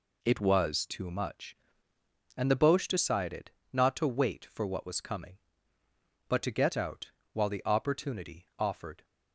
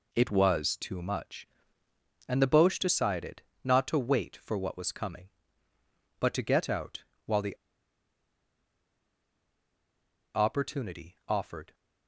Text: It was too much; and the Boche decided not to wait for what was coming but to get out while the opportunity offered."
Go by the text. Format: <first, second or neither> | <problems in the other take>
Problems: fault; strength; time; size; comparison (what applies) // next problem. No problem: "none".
first | pauses between "decided" and "not"; slight; at 3.4 s; 0.20 s long; slight in the first // pauses between "out" and "while"; slight; at 7.0 s; 0.22 s long; slight in the first // pauses between "the" and "opportunity"; strong; at 7.5 s; 2.7 s long